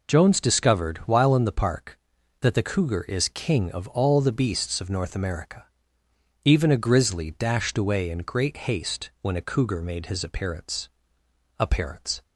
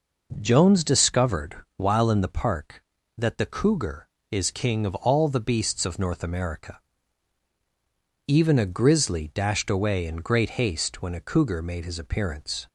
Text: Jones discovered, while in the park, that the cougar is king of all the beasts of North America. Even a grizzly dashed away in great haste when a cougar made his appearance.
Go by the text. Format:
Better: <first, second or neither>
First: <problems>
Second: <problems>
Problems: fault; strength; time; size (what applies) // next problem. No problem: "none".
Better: second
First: says "appearance" twice; at 11.5 s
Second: none